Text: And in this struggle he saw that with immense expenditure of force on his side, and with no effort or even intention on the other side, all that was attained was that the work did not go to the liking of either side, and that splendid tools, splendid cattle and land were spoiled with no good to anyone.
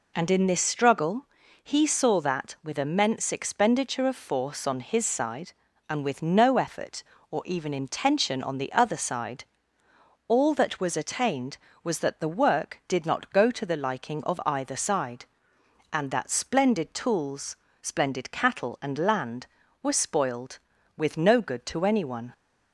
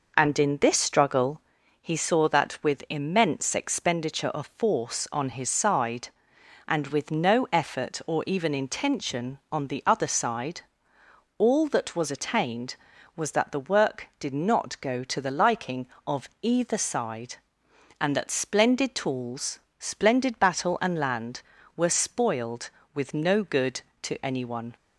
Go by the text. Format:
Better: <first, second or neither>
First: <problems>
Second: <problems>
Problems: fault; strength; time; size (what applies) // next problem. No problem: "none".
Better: first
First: pauses between "struggle" and "he"; slight; at 1.2 s; 0.36 s long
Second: pauses between "struggle" and "he"; at 1.4 s; 0.40 s long // says "battle" for "cattle"; at 20.3 s